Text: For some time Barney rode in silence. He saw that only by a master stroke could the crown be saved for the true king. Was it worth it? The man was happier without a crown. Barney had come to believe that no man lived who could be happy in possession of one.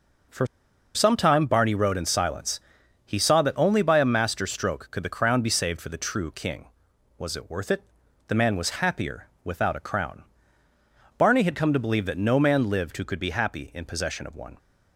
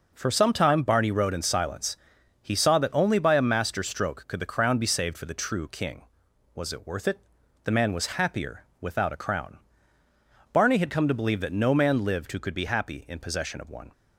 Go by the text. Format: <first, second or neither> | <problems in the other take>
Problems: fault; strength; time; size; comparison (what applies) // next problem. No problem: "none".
second | pauses between "For" and "some"; noticeable; at 0.4 s; 0.49 s long // pauses between "happier" and "without"; slight; at 9.2 s; 0.16 s long; slight in the second